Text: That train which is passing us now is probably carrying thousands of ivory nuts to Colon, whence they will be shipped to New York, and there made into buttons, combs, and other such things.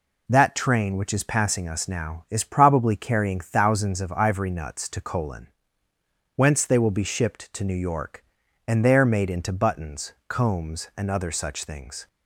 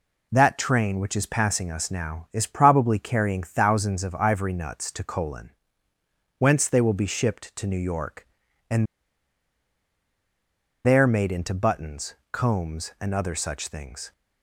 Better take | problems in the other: first | pauses between "and" and "there"; strong; at 8.8 s; 2.0 s long

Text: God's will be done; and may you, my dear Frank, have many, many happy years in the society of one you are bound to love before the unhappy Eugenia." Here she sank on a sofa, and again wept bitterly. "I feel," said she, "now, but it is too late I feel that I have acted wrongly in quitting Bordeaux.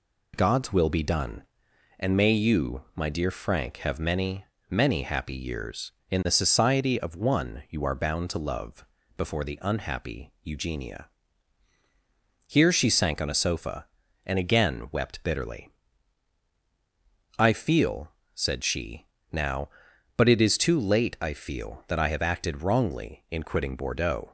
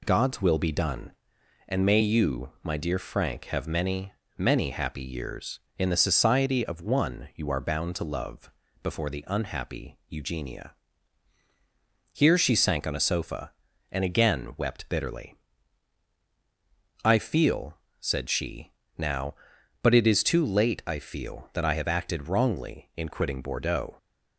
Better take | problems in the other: neither | pauses between "love" and "before"; slight; the same in both

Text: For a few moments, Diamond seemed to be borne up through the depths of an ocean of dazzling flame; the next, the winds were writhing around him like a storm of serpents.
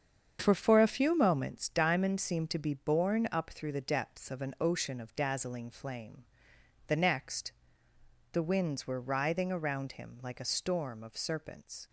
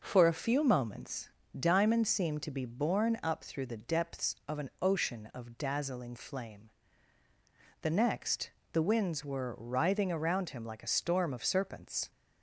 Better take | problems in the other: second | starts louder than the rest; strong; until 1.4 s; 7.5 dB // says "For" twice; at 0.5 s

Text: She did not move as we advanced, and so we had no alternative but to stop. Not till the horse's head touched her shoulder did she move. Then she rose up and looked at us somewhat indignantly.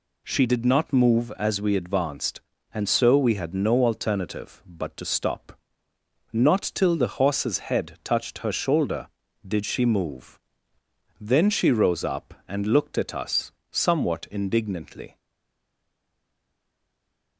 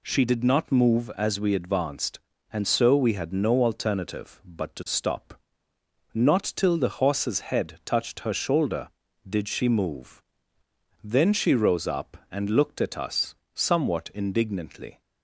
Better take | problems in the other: second | pauses between "us" and "somewhat"; slight; at 13.5 s; 0.18 s long; slight in the second // stays silent after the last word; from 15.1 s on; 2.2 s long

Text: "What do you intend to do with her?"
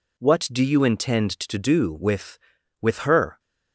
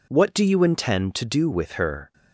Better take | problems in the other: second | says "with" twice; at 2.8 s

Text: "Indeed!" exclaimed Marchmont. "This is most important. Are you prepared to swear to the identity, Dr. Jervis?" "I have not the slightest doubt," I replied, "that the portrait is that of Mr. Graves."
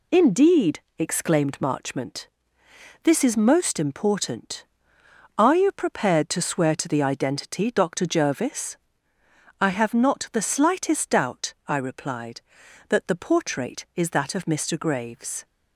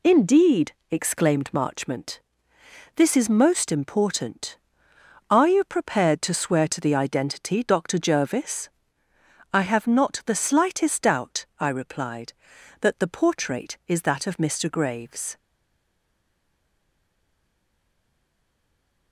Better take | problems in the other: first | stays silent after the last word; strong; from 15.3 s on; 3.8 s long

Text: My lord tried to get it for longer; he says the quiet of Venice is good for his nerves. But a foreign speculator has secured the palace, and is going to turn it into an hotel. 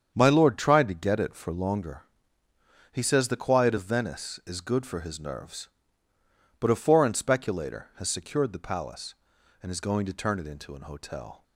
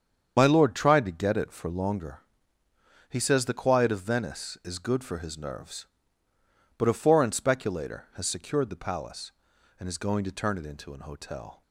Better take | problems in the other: first | loses the start of "My"; at 0.3 s; 45 ms // starts louder than the rest; strong; until 1.3 s; 7.5 dB; strong in the first

